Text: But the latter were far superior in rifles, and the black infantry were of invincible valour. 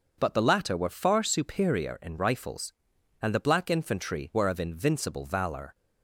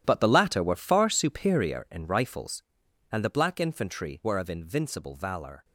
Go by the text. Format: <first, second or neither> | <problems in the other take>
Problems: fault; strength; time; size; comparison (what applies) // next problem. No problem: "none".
first | gets quieter; strong; throughout; 14 dB // starts louder than the rest; strong; until 1.0 s; 11.5 dB; also in the first